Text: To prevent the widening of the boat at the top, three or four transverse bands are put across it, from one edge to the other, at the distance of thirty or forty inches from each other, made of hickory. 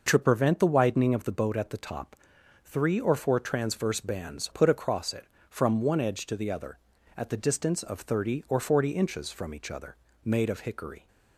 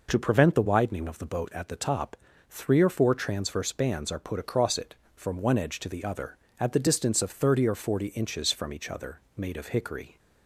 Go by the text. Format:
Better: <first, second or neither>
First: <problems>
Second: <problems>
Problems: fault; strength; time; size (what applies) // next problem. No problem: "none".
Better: second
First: skips "are"; at 4.5 s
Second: none